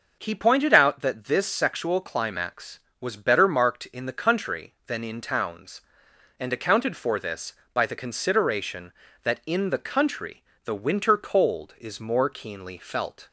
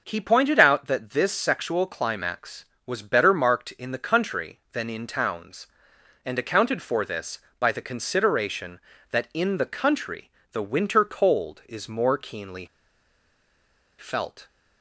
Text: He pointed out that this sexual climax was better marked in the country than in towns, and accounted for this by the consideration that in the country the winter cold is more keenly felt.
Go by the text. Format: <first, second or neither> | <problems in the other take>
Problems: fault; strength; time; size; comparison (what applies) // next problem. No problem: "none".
first | pauses between "country" and "the"; slight; at 10.2 s; 0.22 s long; slight in the first // pauses between "keenly" and "felt"; strong; at 12.6 s; 1.3 s long